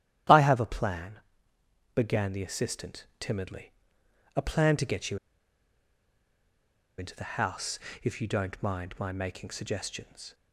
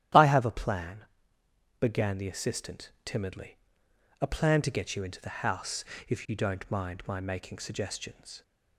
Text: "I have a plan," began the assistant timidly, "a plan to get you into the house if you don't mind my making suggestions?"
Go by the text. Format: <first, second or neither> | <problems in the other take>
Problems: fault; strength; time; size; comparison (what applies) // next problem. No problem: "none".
second | starts louder than the rest; strong; until 2.0 s; 11 dB; strong in the second // pauses between "you" and "into"; strong; at 5.1 s; 1.8 s long // pauses between "house" and "if"; slight; at 7.7 s; 0.24 s long; slight in the second